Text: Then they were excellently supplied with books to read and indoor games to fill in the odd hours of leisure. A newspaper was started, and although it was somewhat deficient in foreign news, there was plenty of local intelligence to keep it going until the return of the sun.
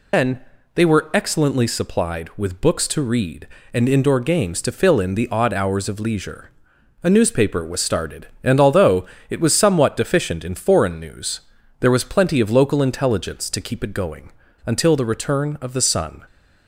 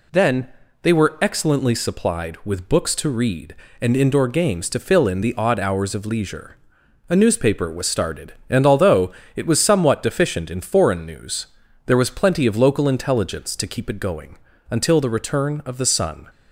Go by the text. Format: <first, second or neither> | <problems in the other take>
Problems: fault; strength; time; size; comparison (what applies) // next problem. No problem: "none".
second | loses the start of "Then"; at 0.1 s; 95 ms // pauses between "Then" and "they"; slight; at 0.4 s; 0.32 s long; slight in the second // pauses between "although" and "it"; slight; at 9.0 s; 0.22 s long; slight in the second // pauses between "going" and "until"; slight; at 14.3 s; 0.33 s long; slight in the second